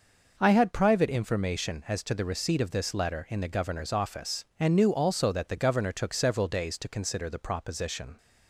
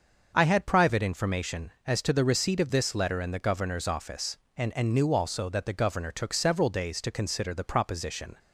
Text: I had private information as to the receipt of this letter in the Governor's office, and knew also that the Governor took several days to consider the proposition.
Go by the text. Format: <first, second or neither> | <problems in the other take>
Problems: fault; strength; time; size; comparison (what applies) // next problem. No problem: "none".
first | starts louder than the rest; until 1.3 s; 6.5 dB // says "and" twice; at 4.7 s